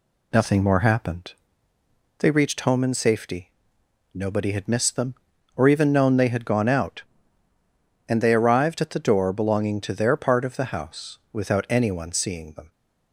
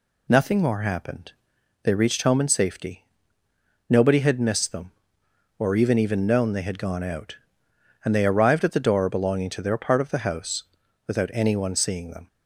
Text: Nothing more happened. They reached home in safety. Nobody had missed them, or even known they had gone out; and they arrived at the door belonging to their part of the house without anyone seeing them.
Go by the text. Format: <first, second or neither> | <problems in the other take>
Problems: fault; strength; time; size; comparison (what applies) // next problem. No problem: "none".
first | says "even" twice; at 5.9 s // pauses between "house" and "without"; at 10.6 s; 0.44 s long